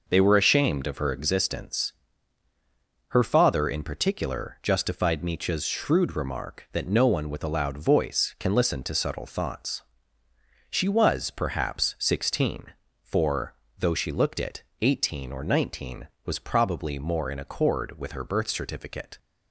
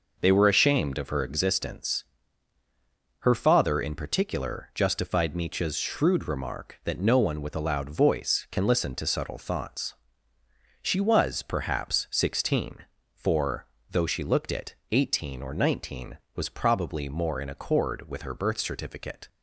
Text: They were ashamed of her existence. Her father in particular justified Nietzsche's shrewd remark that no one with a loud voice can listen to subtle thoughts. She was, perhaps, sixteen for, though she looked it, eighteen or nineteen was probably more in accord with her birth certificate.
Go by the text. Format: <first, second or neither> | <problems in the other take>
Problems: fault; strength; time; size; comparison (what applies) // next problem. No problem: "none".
neither | none